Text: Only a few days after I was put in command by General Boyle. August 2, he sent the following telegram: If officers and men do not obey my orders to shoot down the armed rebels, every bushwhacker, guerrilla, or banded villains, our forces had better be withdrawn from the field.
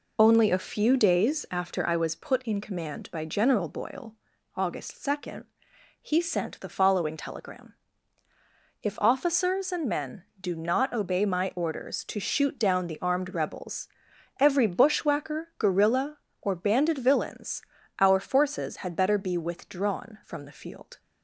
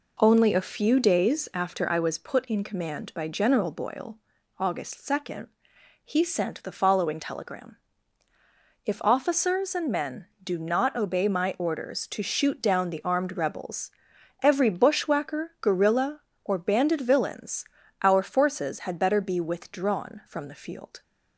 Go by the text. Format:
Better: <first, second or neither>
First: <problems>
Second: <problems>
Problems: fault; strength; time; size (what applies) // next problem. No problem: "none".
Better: second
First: loses the start of "Only"; at 0.1 s; 45 ms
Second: none